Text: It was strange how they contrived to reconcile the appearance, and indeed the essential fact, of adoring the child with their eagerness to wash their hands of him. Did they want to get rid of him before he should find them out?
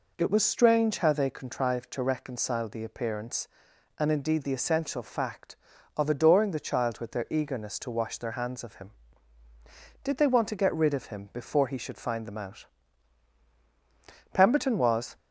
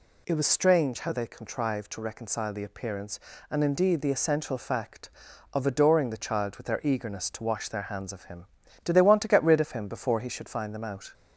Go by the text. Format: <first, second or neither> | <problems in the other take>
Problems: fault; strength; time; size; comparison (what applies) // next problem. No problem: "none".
second | goes on to say "Pemberton was"; noticeable; from 14.3 s on; 0.82 s long